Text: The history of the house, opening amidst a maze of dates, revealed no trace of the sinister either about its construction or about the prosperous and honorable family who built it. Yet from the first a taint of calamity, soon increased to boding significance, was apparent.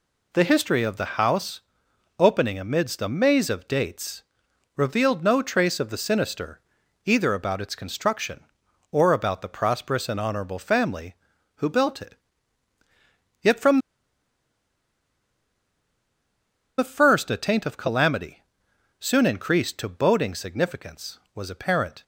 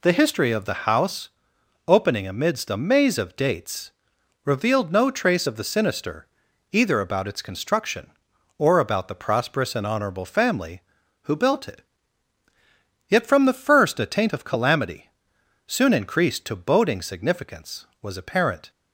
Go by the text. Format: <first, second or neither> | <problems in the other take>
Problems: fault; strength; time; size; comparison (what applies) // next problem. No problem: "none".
second | pauses between "sinister" and "either"; at 6.5 s; 0.44 s long; also in the second // pauses between "from" and "the"; strong; at 13.7 s; 2.9 s long